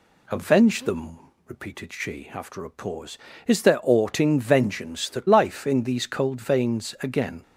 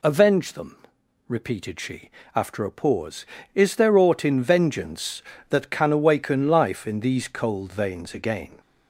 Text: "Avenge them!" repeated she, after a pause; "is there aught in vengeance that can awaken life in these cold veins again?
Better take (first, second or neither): second